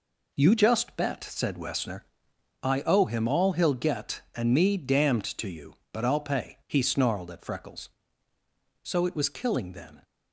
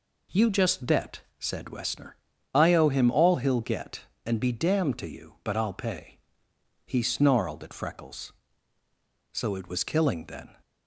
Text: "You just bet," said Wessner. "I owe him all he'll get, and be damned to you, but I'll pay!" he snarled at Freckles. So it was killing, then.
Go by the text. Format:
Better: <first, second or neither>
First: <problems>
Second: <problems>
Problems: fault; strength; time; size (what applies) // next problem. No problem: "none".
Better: second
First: says "me" for "be"; at 4.5 s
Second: none